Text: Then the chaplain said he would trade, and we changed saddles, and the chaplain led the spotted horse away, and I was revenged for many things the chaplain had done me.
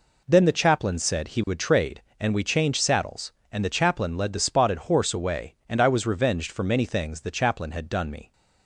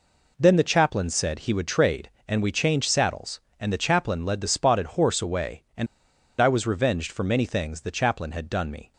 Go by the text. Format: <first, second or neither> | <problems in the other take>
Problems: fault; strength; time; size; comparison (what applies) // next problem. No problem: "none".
first | pauses between "and" and "I"; noticeable; at 5.8 s; 0.53 s long